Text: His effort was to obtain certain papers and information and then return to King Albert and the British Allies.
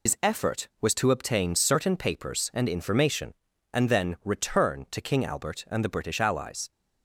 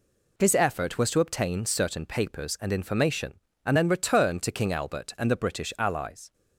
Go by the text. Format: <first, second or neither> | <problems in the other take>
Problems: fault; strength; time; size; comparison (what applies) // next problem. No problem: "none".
second | loses the start of "His"; at 0.0 s; 85 ms